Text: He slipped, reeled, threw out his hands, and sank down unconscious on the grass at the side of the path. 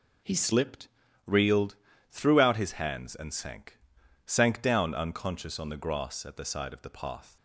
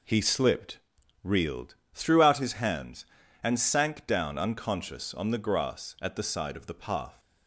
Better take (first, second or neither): second